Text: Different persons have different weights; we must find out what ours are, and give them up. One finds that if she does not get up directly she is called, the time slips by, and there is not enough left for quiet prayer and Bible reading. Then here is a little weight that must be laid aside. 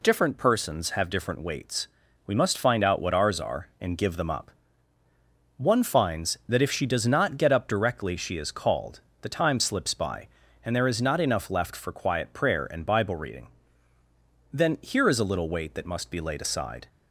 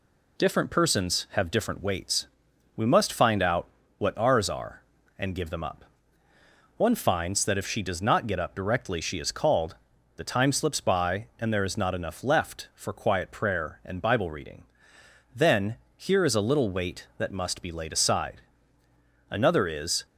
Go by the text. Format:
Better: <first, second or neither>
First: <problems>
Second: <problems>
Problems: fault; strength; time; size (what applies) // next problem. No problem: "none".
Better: first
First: none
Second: pauses between "out" and "what"; slight; at 3.6 s; 0.32 s long // pauses between "Then" and "here"; slight; at 15.7 s; 0.20 s long // goes on to say "Another is"; noticeable; from 19.3 s on; 0.74 s long